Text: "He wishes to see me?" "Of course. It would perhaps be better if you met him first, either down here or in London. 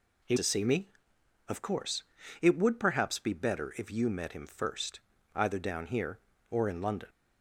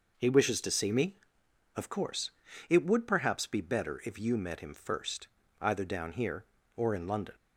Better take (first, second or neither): second